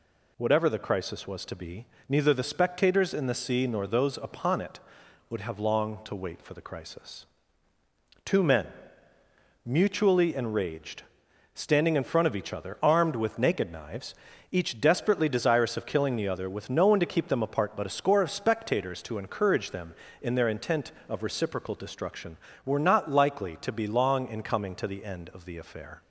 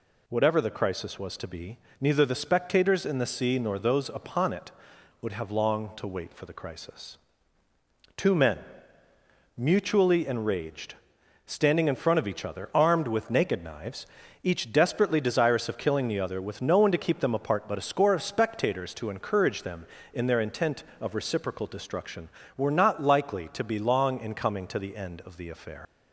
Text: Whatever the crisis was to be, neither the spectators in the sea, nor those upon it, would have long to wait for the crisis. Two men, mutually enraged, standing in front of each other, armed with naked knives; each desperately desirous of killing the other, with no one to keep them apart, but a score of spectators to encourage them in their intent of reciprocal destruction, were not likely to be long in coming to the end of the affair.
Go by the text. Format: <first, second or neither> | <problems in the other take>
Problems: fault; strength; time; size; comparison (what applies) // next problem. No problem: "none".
first | leaves "affair" unfinished; at 25.8 s; 90 ms